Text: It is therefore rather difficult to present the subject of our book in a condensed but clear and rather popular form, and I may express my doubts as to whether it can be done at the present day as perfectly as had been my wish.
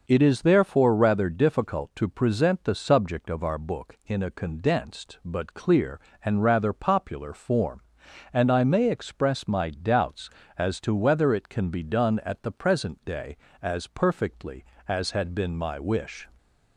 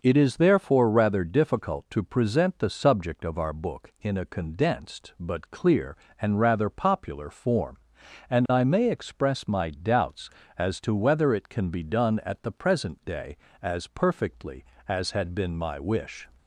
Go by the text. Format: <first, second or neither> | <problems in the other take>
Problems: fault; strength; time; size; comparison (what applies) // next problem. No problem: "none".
neither | none